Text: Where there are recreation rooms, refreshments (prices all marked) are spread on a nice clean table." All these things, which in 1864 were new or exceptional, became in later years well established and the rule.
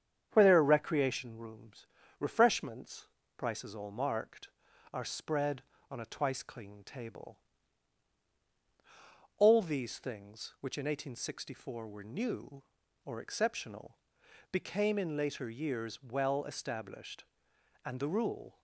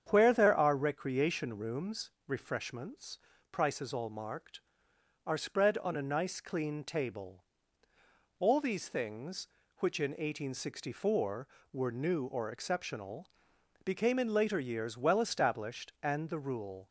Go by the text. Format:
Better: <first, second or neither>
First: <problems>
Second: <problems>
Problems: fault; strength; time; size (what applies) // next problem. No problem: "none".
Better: second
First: starts louder than the rest; strong; until 1.3 s; 8 dB // says "twice" for "nice"; at 6.0 s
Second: starts louder than the rest; strong; until 1.1 s; 8 dB